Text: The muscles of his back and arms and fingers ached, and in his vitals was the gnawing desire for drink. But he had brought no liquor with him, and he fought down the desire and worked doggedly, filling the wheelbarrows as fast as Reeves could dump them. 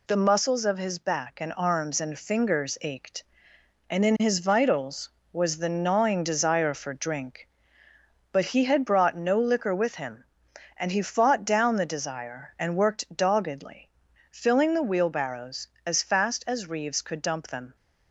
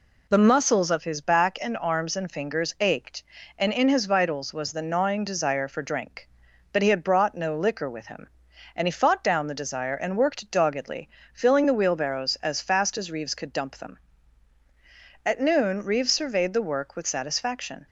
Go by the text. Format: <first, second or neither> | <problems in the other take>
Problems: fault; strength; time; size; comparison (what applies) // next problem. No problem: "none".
first | goes on to say "At noon Reeves surveyed the work with satisfaction"; strong; from 15.2 s on; 2.6 s long